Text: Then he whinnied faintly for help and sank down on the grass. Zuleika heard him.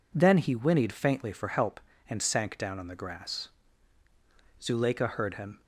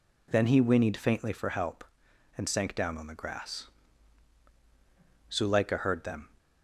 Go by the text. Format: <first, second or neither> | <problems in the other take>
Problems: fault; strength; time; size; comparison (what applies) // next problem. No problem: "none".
first | says "them" for "him"; at 6.0 s